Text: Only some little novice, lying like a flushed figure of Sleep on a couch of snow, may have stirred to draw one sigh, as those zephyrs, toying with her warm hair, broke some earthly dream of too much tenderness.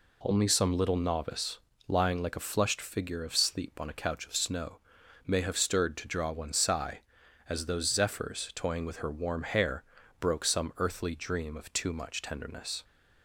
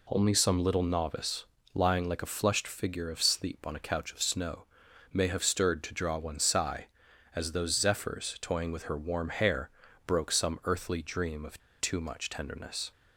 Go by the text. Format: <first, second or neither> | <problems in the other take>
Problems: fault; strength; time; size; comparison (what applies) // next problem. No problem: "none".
first | pauses between "of" and "too"; slight; at 11.5 s; 0.19 s long